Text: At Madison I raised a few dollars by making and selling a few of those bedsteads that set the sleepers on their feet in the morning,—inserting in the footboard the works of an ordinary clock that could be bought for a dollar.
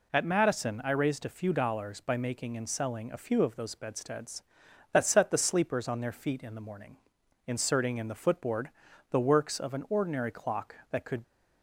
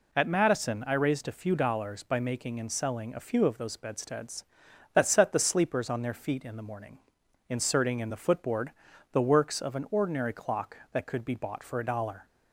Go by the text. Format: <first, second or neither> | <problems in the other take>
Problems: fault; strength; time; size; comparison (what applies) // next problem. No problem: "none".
second | pauses between "footboard" and "the"; at 8.7 s; 0.40 s long; also in the second // stops before "be bought for a dollar"; at 11.2 s